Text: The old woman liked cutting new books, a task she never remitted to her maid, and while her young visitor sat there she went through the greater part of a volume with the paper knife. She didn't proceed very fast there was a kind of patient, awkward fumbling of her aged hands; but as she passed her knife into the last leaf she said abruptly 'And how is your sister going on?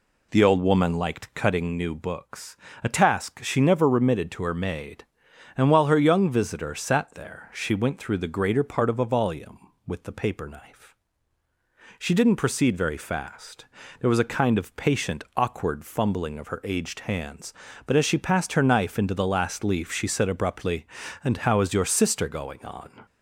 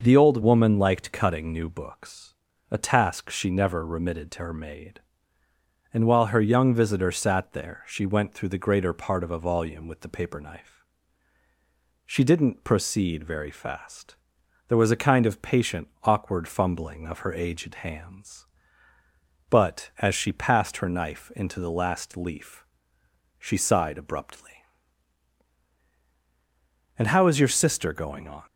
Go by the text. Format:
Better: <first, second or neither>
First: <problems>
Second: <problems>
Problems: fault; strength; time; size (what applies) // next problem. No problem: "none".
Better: first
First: pauses between "fast" and "there"; slight; at 13.6 s; 0.36 s long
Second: pauses between "fast" and "there"; noticeable; at 14.1 s; 0.54 s long // pauses between "leaf" and "she"; noticeable; at 22.6 s; 0.74 s long // says "sighed" for "said"; at 23.5 s